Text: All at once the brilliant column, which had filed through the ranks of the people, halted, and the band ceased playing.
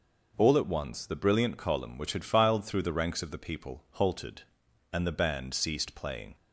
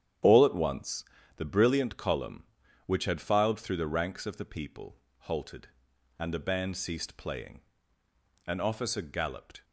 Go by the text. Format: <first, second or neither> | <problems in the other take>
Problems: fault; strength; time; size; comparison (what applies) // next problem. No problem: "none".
first | starts louder than the rest; strong; until 1.5 s; 9.5 dB // pauses between "once" and "the"; slight; at 1.0 s; 0.32 s long // goes on to say "An officer galloped"; noticeable; from 8.4 s on; 1.1 s long